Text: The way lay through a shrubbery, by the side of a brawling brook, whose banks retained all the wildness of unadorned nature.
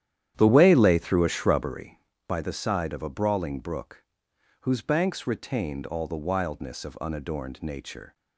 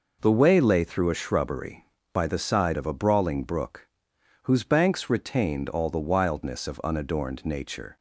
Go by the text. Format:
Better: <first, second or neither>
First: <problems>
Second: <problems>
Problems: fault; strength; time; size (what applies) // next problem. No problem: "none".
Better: second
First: starts louder than the rest; strong; until 1.8 s; 10.5 dB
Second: none